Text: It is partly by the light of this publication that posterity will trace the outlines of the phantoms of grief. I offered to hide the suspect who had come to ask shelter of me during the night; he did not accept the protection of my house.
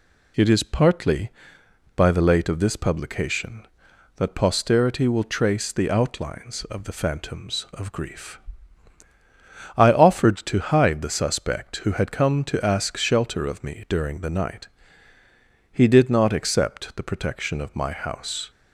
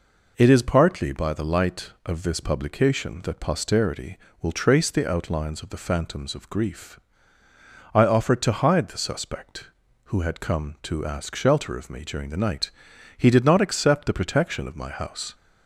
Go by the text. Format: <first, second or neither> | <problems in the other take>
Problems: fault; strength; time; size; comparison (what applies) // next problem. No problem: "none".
second | says "late" for "light"; at 2.2 s